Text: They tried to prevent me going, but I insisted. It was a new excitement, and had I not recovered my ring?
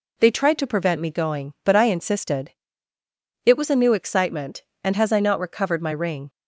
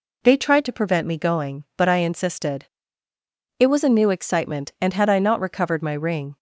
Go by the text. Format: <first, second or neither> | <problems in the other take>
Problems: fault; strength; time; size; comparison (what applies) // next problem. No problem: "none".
second | says "has" for "had"; at 4.9 s